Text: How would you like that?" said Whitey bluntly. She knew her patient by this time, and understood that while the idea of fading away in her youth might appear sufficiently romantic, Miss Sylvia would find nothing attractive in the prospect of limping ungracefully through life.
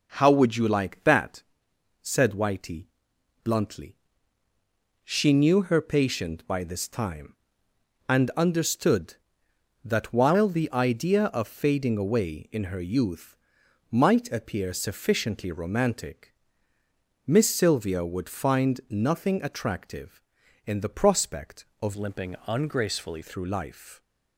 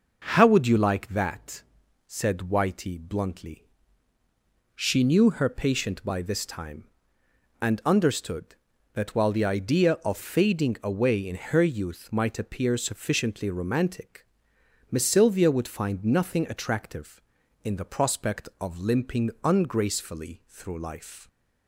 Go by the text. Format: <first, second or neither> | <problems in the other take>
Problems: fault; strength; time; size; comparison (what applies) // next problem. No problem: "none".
second | pauses between "Whitey" and "bluntly"; noticeable; at 2.8 s; 0.58 s long // pauses between "youth" and "might"; noticeable; at 13.3 s; 0.54 s long // changes voice from "limping" to "ungracefully"; from 21.9 to 23.2 s; 1.3 s long